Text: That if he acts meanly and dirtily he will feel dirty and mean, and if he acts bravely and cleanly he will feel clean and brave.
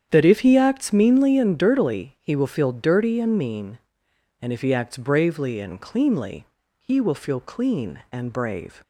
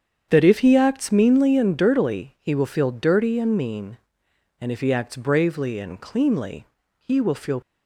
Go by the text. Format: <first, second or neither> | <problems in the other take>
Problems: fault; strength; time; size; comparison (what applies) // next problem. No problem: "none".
first | starts louder than the rest; strong; until 1.3 s; 8 dB; strong in the first // pauses between "cleanly" and "he"; slight; at 6.6 s; 0.34 s long; slight in the first // stops before "clean and brave"; at 7.6 s